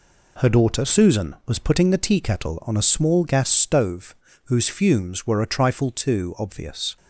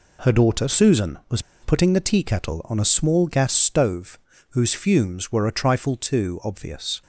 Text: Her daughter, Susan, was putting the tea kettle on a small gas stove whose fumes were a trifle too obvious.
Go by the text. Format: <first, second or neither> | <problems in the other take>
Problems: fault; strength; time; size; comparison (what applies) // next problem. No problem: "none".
first | pauses between "was" and "putting"; slight; at 1.3 s; 0.22 s long // pauses between "stove" and "whose"; slight; at 4.1 s; 0.34 s long; slight in the first